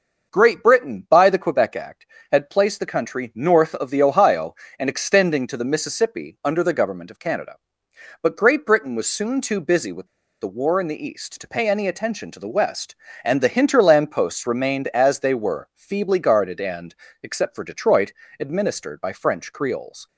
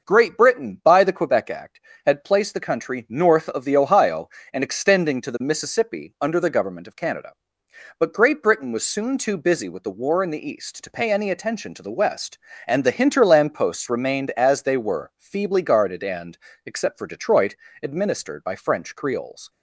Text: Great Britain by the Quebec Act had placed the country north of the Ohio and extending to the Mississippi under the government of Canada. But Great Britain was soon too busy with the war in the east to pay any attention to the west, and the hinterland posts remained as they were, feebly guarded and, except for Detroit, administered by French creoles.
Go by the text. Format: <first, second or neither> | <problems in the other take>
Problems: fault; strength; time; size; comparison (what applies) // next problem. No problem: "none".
second | starts louder than the rest; noticeable; until 1.3 s; 6 dB; noticeable in the second // pauses between "with" and "the"; slight; at 10.0 s; 0.36 s long